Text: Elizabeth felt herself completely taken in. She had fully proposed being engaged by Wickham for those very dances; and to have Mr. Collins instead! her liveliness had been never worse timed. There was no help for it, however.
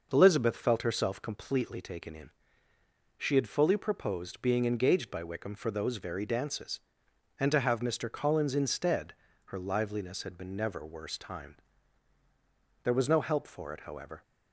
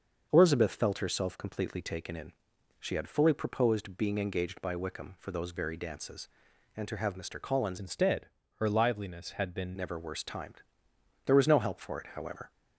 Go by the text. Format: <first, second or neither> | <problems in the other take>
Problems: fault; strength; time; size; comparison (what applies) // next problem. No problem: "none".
first | starts louder than the rest; until 1.3 s; 6.5 dB // changes voice from "instead" to "been"; from 7.7 to 9.7 s; 2.0 s long